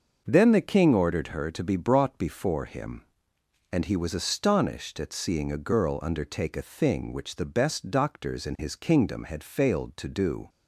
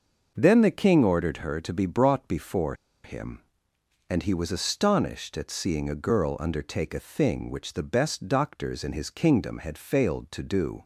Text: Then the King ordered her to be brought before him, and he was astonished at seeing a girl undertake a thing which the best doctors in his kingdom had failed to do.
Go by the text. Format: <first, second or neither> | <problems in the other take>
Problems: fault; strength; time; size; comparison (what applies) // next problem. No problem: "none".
first | pauses between "before" and "him"; slight; at 2.7 s; 0.30 s long